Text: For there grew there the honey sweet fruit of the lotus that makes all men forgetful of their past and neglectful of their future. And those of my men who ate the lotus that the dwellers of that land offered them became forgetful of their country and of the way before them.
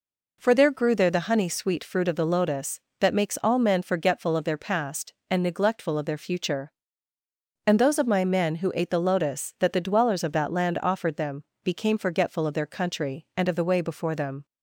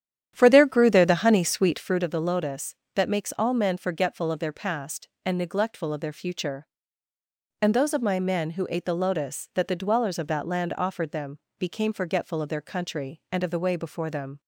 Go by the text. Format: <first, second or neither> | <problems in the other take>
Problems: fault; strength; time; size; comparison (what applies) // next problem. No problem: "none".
first | starts louder than the rest; strong; until 2.1 s; 10 dB // pauses between "them" and "became"; slight; at 11.3 s; 0.22 s long; slight in the first